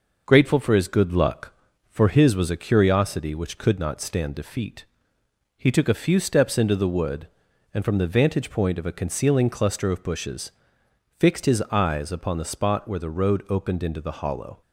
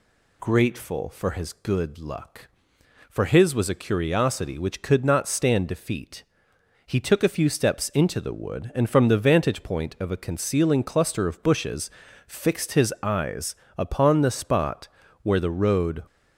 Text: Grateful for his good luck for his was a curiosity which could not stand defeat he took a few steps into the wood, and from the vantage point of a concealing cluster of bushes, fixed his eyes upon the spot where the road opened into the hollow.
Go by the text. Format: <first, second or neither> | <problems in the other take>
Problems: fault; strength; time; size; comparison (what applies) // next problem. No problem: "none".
first | pauses between "defeat" and "he"; noticeable; at 6.2 s; 0.64 s long; noticeable in the first // pauses between "eyes" and "upon"; slight; at 13.5 s; 0.22 s long // pauses between "spot" and "where"; slight; at 14.8 s; 0.34 s long // stops before "opened into the hollow"; at 16.0 s